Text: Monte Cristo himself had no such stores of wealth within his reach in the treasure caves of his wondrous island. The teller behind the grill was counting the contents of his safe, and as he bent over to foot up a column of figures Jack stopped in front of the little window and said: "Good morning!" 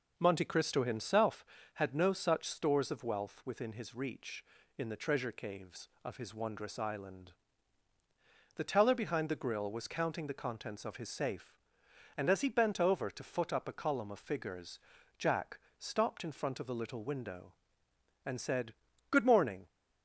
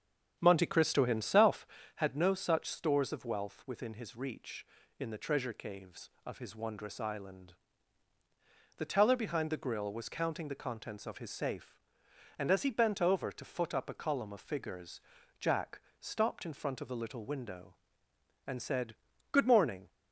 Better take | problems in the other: first | starts louder than the rest; strong; until 2.1 s; 8 dB // pauses between "figures" and "Jack"; at 14.9 s; 0.40 s long; also in the first // pauses between "Jack" and "stopped"; slight; at 15.7 s; 0.20 s long; slight in the first

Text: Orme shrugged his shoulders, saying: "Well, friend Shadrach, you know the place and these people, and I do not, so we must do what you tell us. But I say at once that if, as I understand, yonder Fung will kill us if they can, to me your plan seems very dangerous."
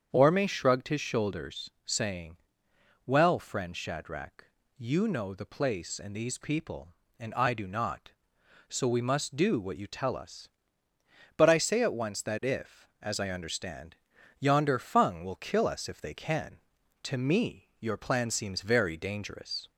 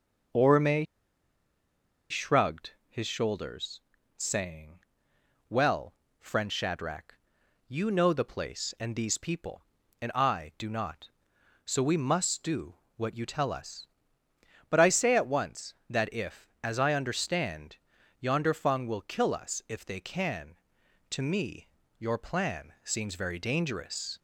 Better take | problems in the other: first | starts louder than the rest; until 2.5 s; 6.5 dB; strong in the first // pauses between "Orme" and "shrugged"; strong; at 0.8 s; 1.2 s long // pauses between "shrugged" and "his"; slight; at 2.7 s; 0.18 s long // pauses between "do" and "what"; slight; at 12.7 s; 0.22 s long // pauses between "me" and "your"; slight; at 21.6 s; 0.30 s long

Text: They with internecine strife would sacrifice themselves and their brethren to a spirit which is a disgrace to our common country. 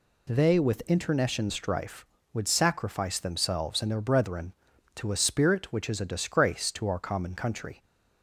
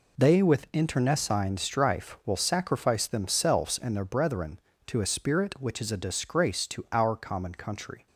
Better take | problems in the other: first | says "will" for "would"; at 2.2 s

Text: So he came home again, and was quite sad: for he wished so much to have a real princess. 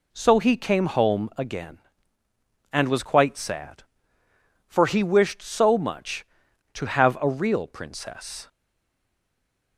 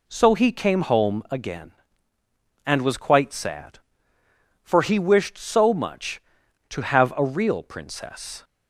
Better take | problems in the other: second | stays silent after the last word; noticeable; from 8.4 s on; 1.3 s long

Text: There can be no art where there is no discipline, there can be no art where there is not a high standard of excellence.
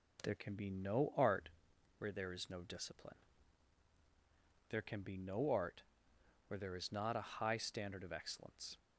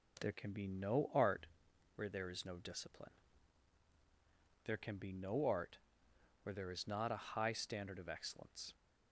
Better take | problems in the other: neither | pauses between "art" and "where"; noticeable; the same in both // pauses between "art" and "where"; noticeable; the same in both

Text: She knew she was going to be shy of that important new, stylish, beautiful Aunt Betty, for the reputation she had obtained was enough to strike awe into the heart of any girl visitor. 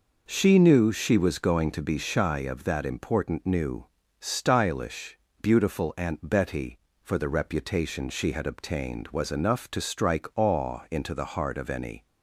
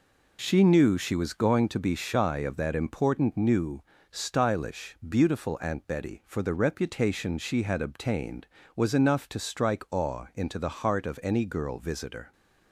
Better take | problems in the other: second | stops before "girl visitor"; at 12.0 s

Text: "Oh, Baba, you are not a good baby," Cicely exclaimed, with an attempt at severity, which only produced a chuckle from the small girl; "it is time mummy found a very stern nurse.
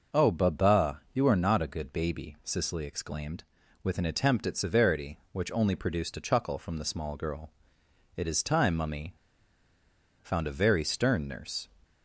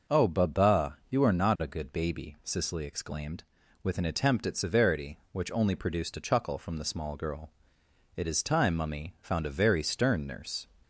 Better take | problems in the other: second | pauses between "mummy" and "found"; at 9.1 s; 1.0 s long

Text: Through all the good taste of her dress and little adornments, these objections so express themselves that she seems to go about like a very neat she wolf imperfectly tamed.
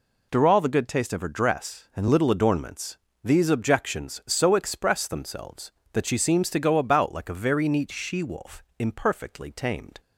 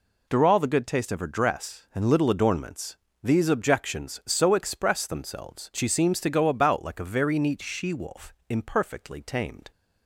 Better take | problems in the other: first | skips "that"; at 5.7 s // pauses between "wolf" and "imperfectly"; slight; at 8.3 s; 0.16 s long; slight in the first

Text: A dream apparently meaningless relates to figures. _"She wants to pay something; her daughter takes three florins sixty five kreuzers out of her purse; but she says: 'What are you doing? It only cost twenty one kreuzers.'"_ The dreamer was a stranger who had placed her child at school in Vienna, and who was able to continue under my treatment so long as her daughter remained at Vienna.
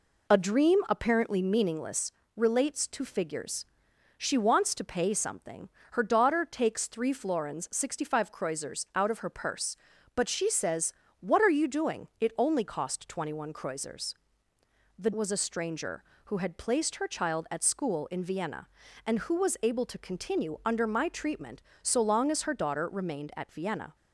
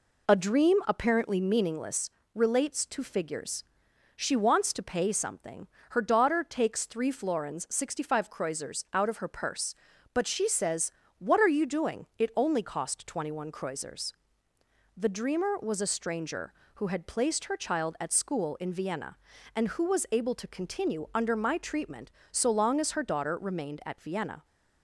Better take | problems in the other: second | pauses between "meaningless" and "relates"; slight; at 2.1 s; 0.24 s long; slight in the second // skips "dreamer"; at 15.1 s

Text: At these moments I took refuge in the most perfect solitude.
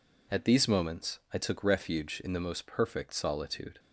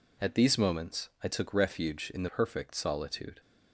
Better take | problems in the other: first | skips "most"; at 2.2 s

